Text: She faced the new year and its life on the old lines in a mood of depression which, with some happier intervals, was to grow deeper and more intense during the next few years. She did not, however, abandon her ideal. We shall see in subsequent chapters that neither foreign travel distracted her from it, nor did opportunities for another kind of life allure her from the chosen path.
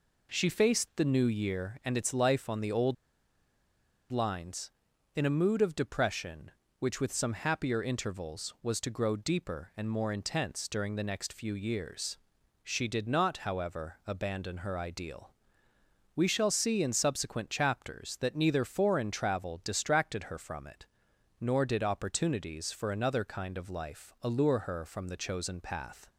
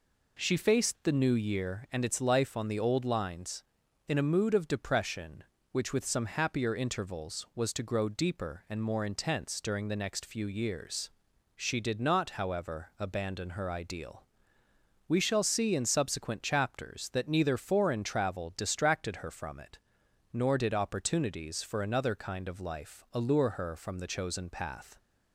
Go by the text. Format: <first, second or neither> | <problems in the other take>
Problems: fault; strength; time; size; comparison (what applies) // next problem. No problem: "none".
second | pauses between "old" and "lines"; at 2.9 s; 1.1 s long